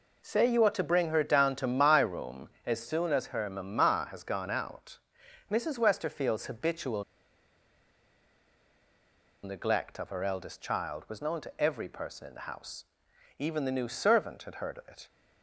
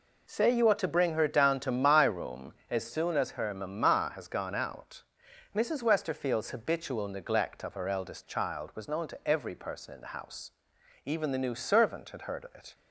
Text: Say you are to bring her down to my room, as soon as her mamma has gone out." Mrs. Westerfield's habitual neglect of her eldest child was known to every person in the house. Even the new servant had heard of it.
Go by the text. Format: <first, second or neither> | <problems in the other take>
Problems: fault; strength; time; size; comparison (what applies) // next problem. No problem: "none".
second | pauses between "habitual" and "neglect"; strong; at 7.0 s; 2.4 s long